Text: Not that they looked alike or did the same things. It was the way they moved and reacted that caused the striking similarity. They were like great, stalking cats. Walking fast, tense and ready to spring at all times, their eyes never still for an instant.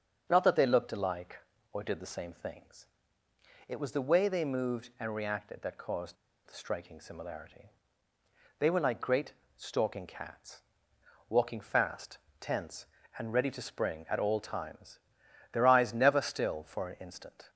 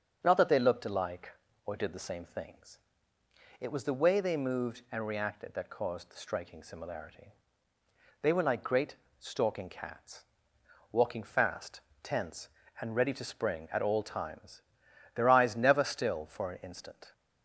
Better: second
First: starts louder than the rest; strong; until 1.3 s; 7 dB // pauses between "caused" and "the"; slight; at 6.1 s; 0.32 s long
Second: starts louder than the rest; strong; until 1.2 s; 7 dB

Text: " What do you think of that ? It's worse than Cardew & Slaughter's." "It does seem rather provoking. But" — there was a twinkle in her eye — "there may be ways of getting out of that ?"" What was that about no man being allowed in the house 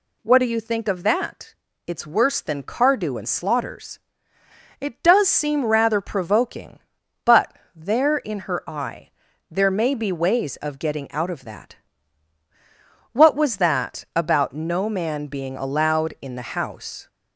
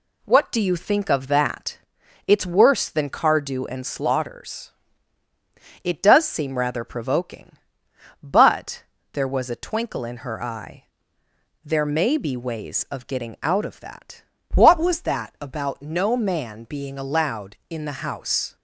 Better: second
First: skips "was a twinkle"; at 8.1 s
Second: none

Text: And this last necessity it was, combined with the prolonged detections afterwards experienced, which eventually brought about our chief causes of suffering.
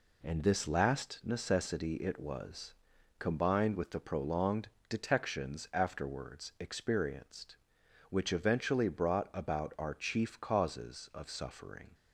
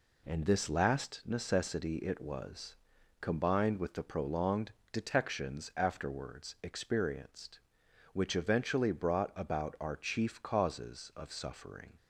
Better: neither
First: pauses between "prolonged" and "detections"; slight; at 4.6 s; 0.22 s long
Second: pauses between "prolonged" and "detections"; slight; at 4.7 s; 0.22 s long

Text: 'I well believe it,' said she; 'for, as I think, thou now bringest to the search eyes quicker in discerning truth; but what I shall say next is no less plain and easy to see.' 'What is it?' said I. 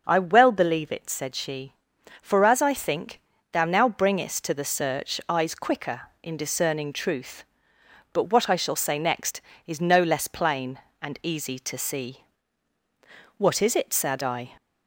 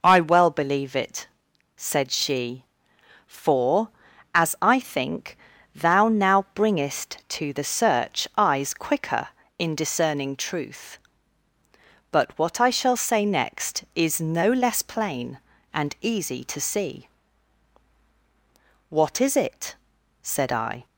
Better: neither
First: none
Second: none

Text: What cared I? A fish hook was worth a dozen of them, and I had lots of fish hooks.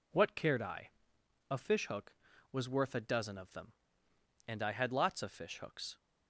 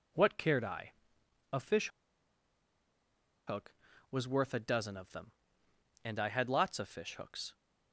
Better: first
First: none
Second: pauses between "fish" and "hook"; strong; at 1.8 s; 1.5 s long

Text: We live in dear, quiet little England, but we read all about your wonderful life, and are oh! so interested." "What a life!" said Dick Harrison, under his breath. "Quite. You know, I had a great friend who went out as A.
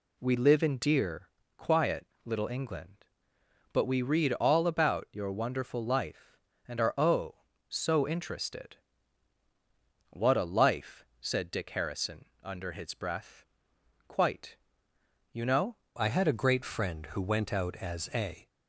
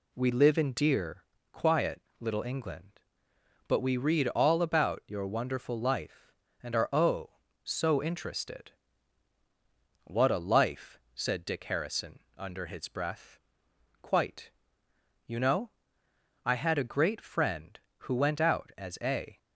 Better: second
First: pauses between "quiet" and "little"; slight; at 2.0 s; 0.18 s long // changes voice at "I"; from 16.0 s on; 2.4 s long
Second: pauses between "quiet" and "little"; slight; at 2.0 s; 0.18 s long

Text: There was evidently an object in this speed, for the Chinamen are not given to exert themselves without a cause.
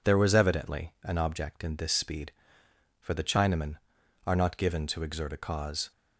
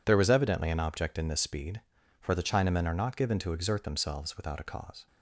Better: second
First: skips "themselves without"; at 5.3 s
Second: none

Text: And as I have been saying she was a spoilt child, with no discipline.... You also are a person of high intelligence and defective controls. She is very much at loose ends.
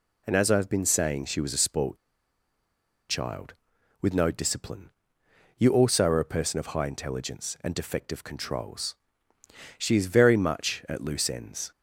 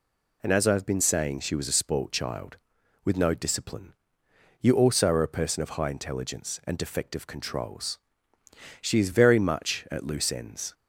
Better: second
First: pauses between "spoilt" and "child"; at 1.9 s; 1.1 s long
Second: none

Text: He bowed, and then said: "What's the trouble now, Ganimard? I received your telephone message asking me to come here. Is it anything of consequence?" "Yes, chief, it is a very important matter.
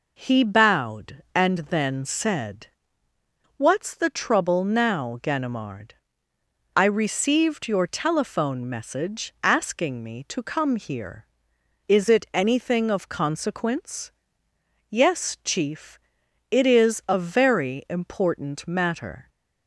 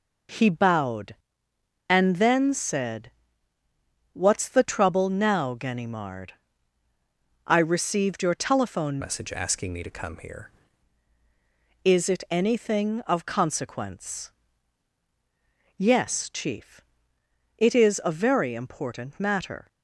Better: first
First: none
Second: changes voice from "message" to "here"; from 9.0 to 10.4 s; 1.4 s long

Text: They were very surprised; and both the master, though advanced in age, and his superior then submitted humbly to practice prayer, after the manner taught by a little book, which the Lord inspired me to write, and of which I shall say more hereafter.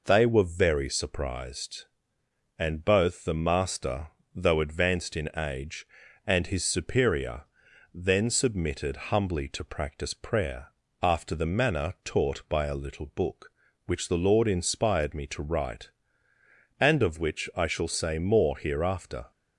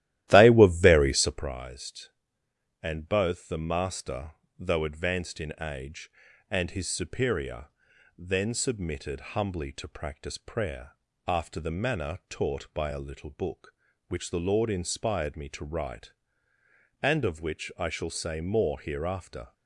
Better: first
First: pauses between "superior" and "then"; noticeable; at 7.4 s; 0.50 s long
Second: starts louder than the rest; strong; until 1.5 s; 14 dB // pauses between "superior" and "then"; noticeable; at 7.6 s; 0.50 s long

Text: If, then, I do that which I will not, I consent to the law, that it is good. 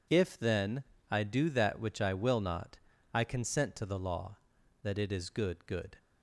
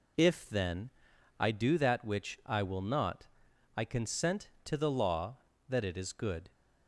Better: second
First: says "good" twice; at 5.6 s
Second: none

